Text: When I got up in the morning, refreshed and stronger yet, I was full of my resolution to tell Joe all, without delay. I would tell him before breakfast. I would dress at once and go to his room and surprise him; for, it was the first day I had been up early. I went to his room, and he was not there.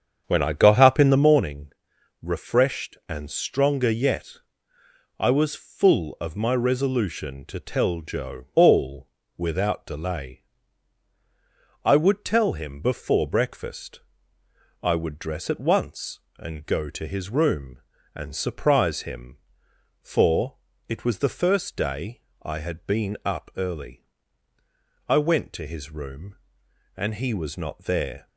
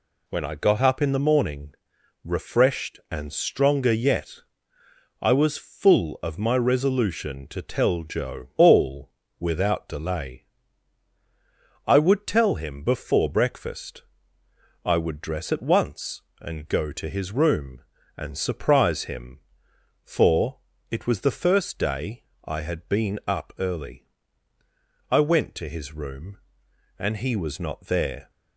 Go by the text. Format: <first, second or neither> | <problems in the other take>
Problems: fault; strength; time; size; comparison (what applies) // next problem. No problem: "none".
second | starts louder than the rest; strong; until 1.5 s; 7.5 dB // pauses between "day" and "I"; slight; at 22.2 s; 0.20 s long; slight in the second